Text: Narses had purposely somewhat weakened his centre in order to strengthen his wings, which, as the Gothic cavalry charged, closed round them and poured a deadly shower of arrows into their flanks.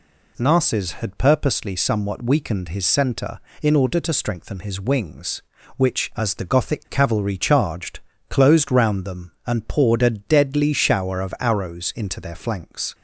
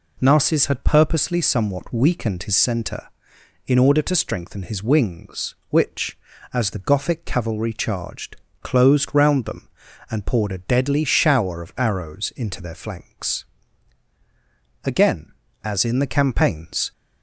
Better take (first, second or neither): first